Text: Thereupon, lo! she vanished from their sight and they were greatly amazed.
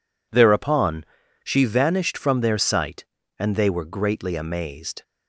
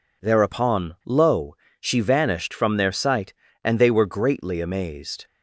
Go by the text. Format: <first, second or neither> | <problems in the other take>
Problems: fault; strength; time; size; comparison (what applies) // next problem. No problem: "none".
second | skips "lo"; at 1.2 s